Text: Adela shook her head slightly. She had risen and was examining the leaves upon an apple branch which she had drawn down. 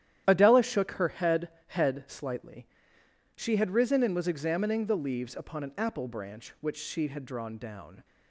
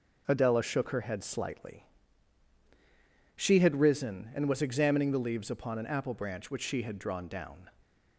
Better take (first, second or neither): second